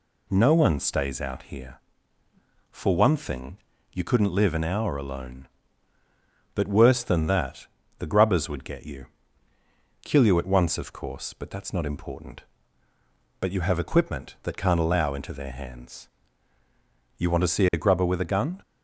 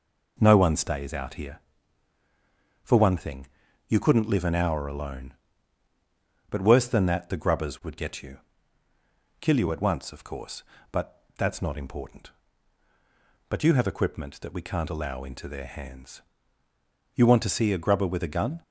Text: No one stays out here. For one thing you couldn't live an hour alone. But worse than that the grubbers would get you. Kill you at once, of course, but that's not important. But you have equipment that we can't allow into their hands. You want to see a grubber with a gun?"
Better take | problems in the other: second | pauses between "thing" and "you"; slight; at 3.5 s; 0.36 s long; also in the second // pauses between "that" and "the"; slight; at 7.6 s; 0.32 s long // skips "we"; at 14.5 s

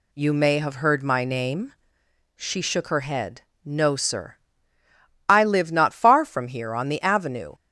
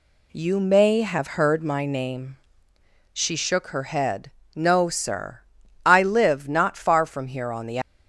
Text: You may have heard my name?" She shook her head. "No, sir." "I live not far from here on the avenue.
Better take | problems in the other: first | stops before "avenue"; at 7.8 s

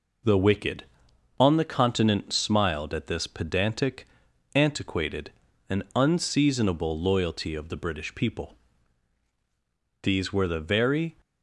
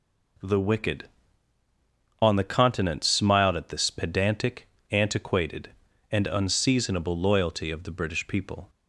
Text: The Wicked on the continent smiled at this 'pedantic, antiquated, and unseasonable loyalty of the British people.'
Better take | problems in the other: second | goes on to say "These were the very"; noticeable; from 10.0 s on; 1.1 s long

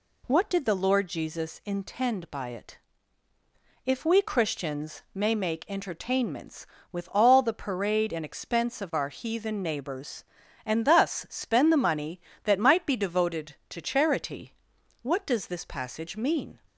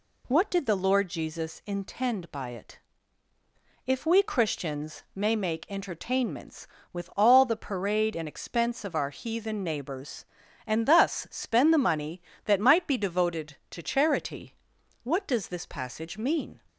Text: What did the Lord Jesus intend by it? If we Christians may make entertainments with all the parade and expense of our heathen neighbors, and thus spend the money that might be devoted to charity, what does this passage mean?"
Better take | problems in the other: neither | none

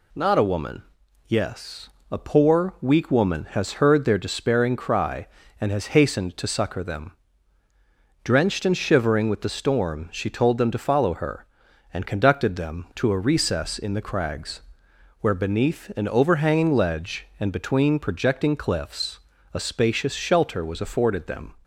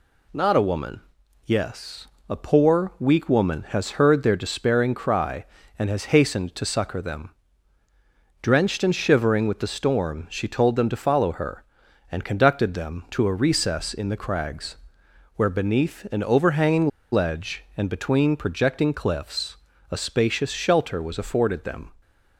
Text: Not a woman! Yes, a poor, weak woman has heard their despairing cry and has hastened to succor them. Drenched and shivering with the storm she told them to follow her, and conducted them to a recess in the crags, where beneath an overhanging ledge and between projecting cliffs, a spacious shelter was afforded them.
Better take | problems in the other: first | pauses between "overhanging" and "ledge"; slight; at 16.8 s; 0.23 s long

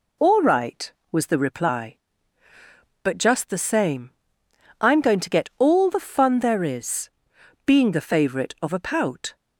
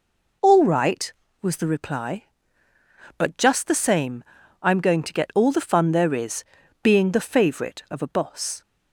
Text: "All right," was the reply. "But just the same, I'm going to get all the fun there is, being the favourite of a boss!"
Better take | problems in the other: second | says "pout" for "boss"; at 8.7 s

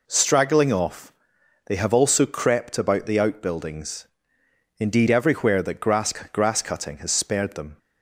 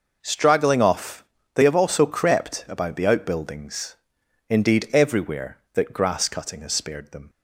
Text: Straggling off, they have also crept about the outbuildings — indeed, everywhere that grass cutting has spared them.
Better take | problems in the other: second | says "grass" twice; at 6.1 s

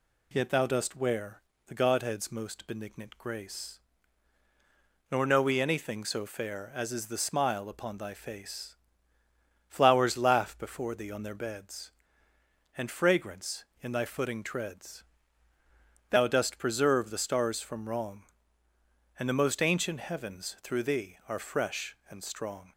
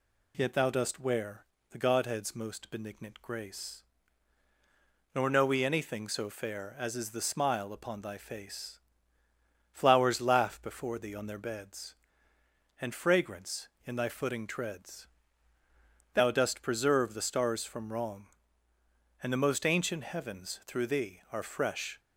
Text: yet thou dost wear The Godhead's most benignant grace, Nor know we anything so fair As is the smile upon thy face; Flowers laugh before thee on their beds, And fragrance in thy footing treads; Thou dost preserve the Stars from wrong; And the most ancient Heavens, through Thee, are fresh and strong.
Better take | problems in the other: first | pauses between "wear" and "The"; slight; at 1.4 s; 0.26 s long; slight in the first // stops before "and strong"; at 21.9 s

